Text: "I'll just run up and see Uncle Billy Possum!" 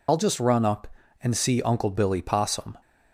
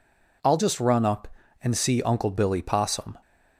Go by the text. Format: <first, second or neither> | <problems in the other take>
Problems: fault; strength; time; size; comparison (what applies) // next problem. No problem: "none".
second | loses the start of "I'll"; at 0.0 s; 70 ms